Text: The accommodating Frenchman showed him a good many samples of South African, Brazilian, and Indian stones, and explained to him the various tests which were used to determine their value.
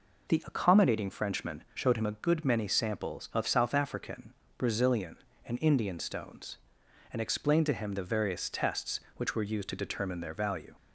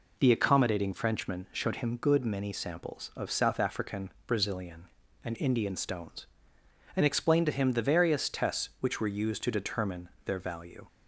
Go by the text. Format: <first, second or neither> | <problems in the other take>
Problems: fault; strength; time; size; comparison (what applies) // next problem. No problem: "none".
first | skips "a"; at 1.9 s // pauses between "determine" and "their"; slight; at 10.0 s; 0.16 s long